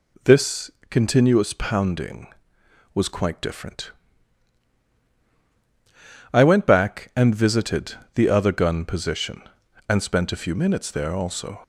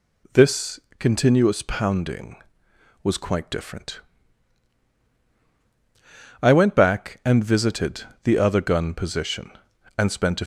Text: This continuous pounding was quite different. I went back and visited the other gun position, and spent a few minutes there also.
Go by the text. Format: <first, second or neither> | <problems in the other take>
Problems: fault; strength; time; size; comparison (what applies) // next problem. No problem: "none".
first | pauses between "This" and "continuous"; slight; at 0.7 s; 0.20 s long; slight in the first // pauses between "visited" and "the"; slight; at 8.0 s; 0.18 s long; slight in the first // stops before "few minutes there also"; at 10.4 s